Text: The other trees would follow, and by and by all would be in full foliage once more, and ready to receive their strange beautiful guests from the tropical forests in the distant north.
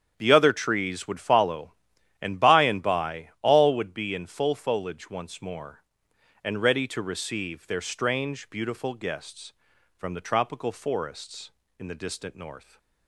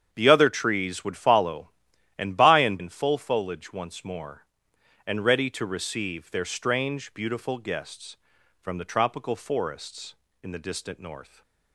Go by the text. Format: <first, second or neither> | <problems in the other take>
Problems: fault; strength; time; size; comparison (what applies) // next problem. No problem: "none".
first | starts louder than the rest; strong; until 1.1 s; 8 dB; strong in the first // skips "by all would be"; at 2.7 s // stays silent after the last word; slight; from 11.2 s on; 0.5 s long